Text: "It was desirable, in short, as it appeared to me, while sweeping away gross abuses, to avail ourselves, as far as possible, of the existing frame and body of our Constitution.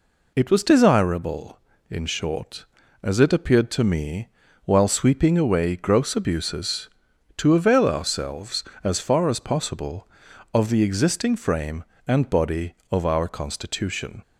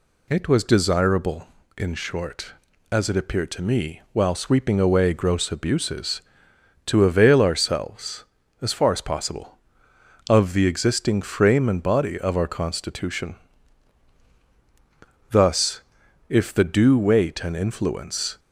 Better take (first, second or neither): first